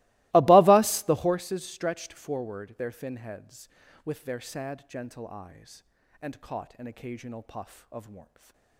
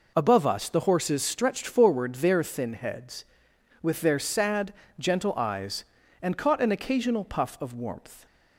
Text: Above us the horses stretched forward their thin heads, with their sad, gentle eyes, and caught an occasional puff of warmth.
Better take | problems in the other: second | starts louder than the rest; strong; until 1.4 s; 21.5 dB // stays silent after the last word; slight; from 8.2 s on; 0.5 s long

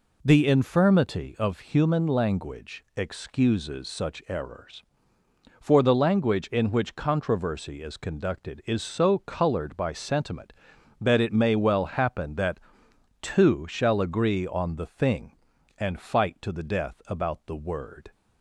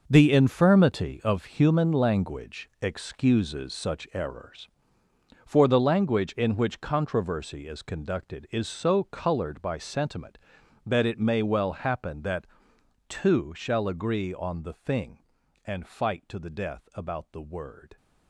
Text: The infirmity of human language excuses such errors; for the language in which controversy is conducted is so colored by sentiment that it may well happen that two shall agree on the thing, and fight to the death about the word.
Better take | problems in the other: first | gets quieter; strong; throughout; 12 dB // pauses between "that" and "two"; noticeable; at 12.4 s; 0.62 s long; noticeable in the first

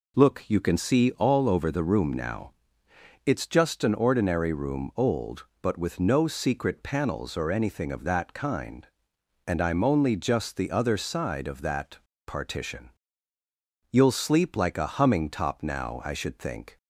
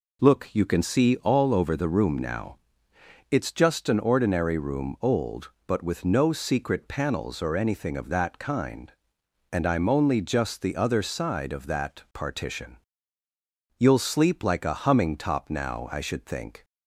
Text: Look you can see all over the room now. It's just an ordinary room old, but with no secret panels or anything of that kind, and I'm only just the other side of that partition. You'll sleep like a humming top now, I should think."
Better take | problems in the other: second | pauses between "that" and "partition"; slight; at 11.9 s; 0.28 s long

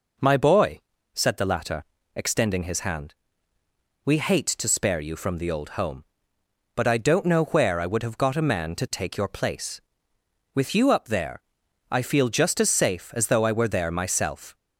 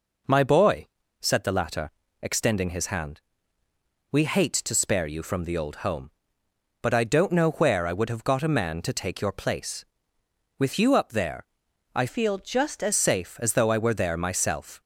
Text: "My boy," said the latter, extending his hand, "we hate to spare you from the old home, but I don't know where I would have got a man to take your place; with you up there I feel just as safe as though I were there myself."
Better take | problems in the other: first | pauses between "there" and "I"; noticeable; at 11.4 s; 0.50 s long; noticeable in the first // changes voice from "feel" to "as"; from 12.0 to 12.9 s; 0.9 s long

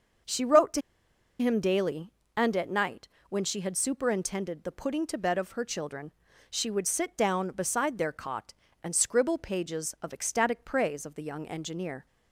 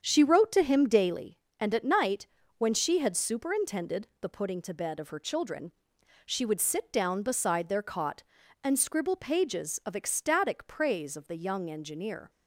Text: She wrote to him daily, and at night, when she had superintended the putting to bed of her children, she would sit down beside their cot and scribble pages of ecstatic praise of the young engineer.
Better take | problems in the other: second | starts louder than the rest; until 1.8 s; 6.5 dB; strong in the second // pauses between "to" and "him"; noticeable; at 0.8 s; 0.58 s long

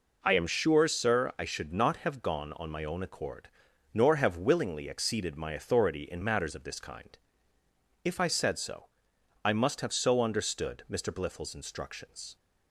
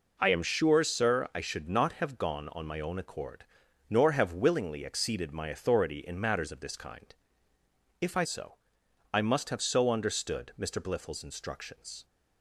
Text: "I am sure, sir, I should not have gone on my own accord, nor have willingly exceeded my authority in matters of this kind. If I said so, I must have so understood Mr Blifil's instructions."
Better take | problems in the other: first | skips "said"; at 8.2 s

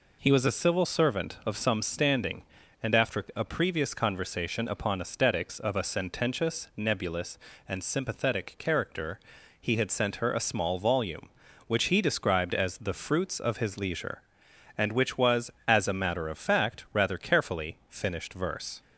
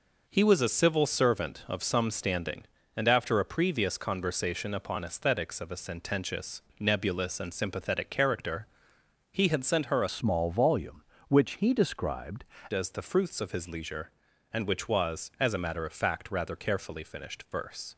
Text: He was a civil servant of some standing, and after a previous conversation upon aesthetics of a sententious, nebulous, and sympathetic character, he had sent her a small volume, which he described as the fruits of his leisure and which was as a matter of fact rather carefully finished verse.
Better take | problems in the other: first | changes voice from "small" to "described"; from 10.0 to 12.4 s; 2.4 s long

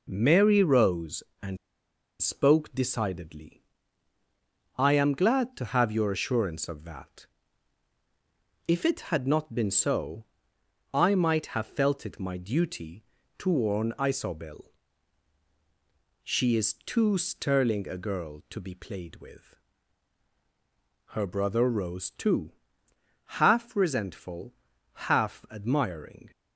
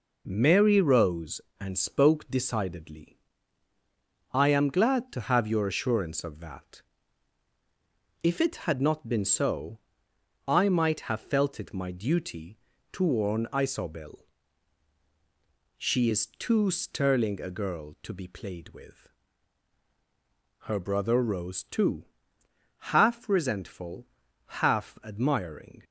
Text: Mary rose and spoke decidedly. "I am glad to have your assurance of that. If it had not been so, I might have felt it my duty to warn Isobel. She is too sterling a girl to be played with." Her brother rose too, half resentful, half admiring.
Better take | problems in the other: second | pauses between "and" and "spoke"; noticeable; at 1.5 s; 0.65 s long

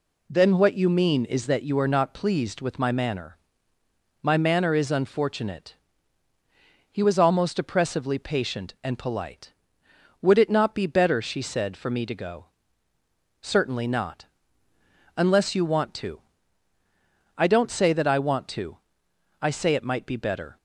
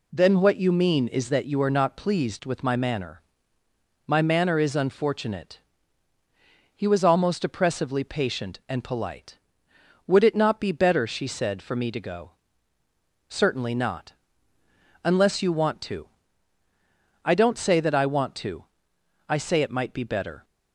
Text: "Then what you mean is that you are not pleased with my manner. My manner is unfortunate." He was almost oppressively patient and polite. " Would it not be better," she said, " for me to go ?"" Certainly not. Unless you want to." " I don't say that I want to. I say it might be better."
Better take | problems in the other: neither | none

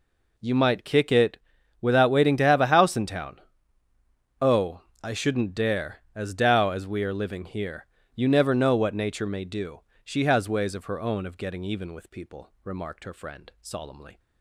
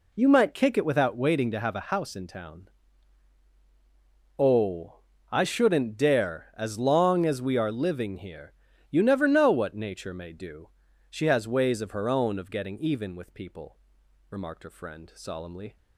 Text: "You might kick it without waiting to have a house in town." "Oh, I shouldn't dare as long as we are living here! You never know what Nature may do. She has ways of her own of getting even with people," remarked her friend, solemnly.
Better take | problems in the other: second | pauses between "it" and "without"; at 1.3 s; 0.42 s long // says "dao" for "long"; at 6.3 s

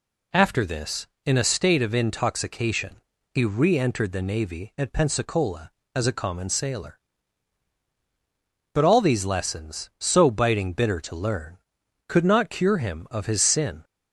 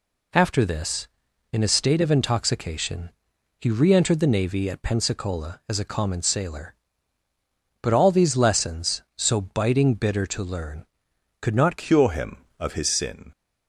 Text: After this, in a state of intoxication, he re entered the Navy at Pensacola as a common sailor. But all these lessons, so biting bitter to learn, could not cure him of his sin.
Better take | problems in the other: first | changes voice at "cure"; from 11.7 s on; 1.5 s long

